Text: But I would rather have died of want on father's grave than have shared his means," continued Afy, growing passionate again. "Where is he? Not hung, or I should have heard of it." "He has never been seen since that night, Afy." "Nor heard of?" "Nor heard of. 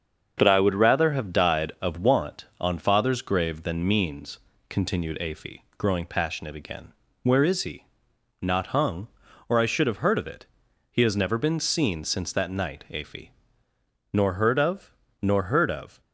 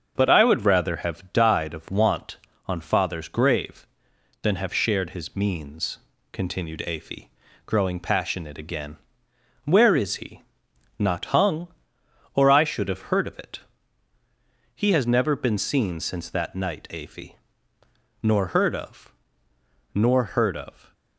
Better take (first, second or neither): second